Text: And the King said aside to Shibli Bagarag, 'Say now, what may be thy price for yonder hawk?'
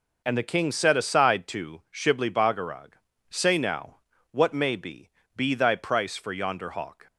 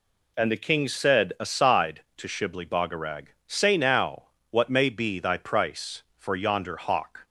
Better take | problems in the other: second | says "be" twice; at 5.3 s

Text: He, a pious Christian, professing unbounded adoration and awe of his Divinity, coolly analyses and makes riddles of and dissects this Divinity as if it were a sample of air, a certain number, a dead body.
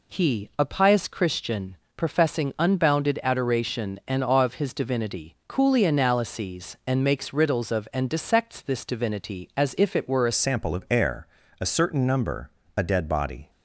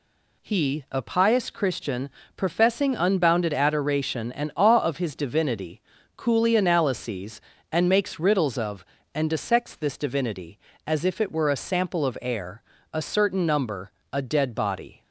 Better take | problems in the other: second | changes voice at "sample"; from 10.3 s on; 3.1 s long

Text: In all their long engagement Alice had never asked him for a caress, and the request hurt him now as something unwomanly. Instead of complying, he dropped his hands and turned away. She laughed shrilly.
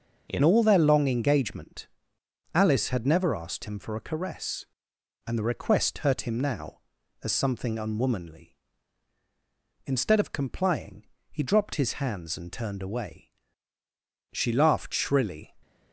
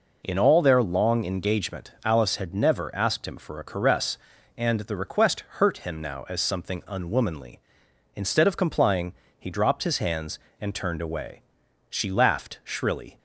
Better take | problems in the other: second | starts louder than the rest; until 1.3 s; 6.5 dB // changes voice at "all"; from 0.4 s on; 15.0 s long // pauses between "engagement" and "Alice"; noticeable; at 1.8 s; 0.68 s long

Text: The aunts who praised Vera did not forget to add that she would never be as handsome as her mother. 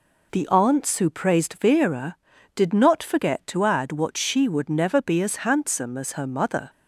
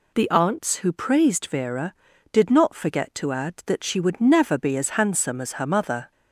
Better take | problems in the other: second | says "what" for "that"; at 3.9 s

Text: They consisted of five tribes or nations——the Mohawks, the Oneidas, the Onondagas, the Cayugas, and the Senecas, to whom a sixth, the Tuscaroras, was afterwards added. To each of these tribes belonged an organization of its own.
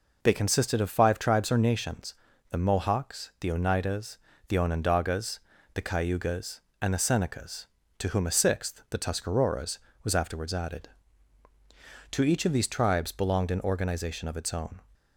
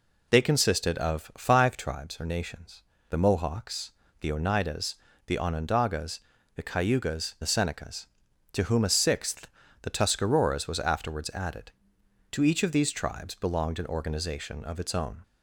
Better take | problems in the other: first | skips "and"; at 7.3 s

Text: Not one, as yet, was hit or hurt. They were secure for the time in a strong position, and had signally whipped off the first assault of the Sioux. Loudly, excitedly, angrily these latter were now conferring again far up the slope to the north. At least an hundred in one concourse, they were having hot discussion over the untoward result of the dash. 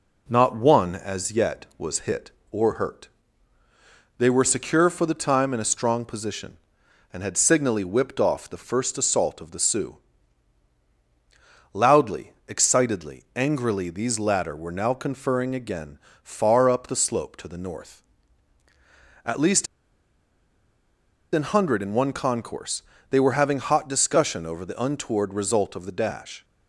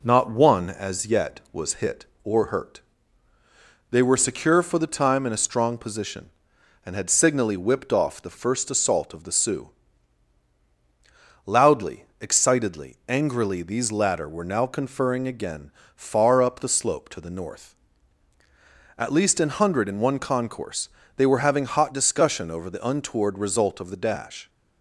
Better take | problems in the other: second | pauses between "again" and "far"; slight; at 15.9 s; 0.24 s long; slight in the second // pauses between "least" and "an"; strong; at 19.6 s; 1.6 s long

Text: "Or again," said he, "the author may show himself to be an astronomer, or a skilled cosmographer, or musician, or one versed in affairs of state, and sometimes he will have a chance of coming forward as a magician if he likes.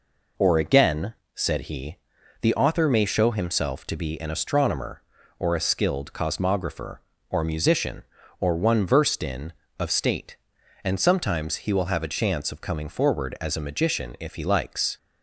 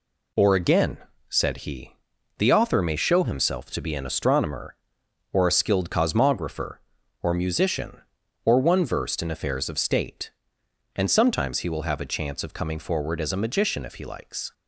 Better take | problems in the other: second | skips "affairs"; at 9.6 s

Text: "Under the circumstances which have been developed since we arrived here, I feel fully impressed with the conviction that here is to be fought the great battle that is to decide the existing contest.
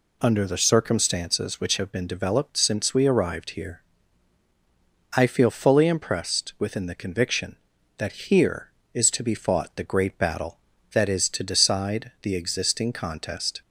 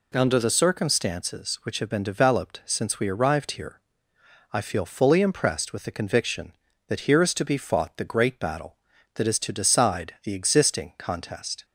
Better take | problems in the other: second | says "within" for "with"; at 6.5 s

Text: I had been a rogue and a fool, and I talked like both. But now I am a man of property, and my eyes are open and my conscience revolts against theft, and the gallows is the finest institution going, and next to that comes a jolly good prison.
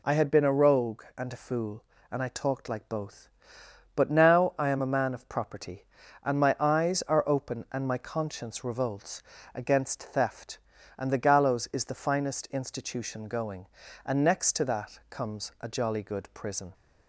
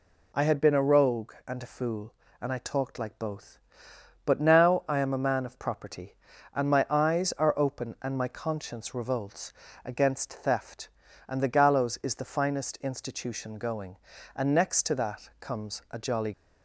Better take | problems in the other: first | pauses between "revolts" and "against"; slight; at 9.5 s; 0.32 s long; slight in the first // stops before "good prison"; at 16.3 s

